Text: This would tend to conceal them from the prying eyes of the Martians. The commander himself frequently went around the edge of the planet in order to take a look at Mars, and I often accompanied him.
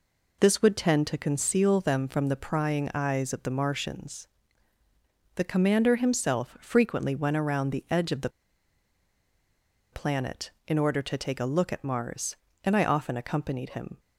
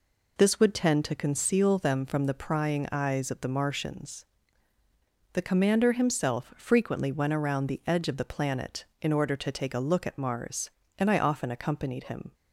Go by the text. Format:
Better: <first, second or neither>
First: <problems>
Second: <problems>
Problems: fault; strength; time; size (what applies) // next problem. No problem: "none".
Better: second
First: pauses between "the" and "planet"; strong; at 8.2 s; 1.6 s long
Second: none